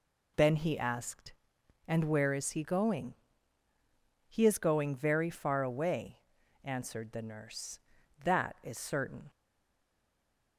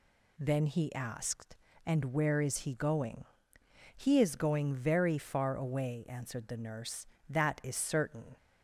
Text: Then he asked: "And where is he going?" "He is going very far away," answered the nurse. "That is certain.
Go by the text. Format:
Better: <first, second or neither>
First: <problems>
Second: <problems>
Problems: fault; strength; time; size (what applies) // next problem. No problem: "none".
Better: second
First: stays silent after the last word; noticeable; from 9.2 s on; 1.3 s long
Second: none